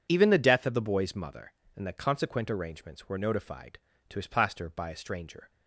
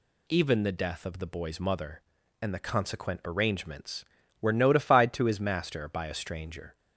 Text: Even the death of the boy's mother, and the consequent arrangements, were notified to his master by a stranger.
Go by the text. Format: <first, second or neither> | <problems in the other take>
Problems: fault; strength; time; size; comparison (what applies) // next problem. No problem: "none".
second | says "plaster" for "master"; at 4.2 s